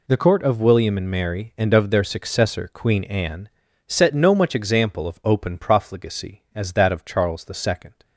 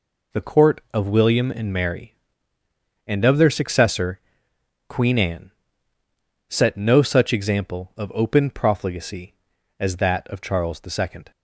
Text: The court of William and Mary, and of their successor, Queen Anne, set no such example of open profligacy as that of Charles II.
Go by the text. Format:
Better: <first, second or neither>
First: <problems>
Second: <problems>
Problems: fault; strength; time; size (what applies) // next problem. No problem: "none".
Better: second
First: says "much" for "such"; at 4.3 s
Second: none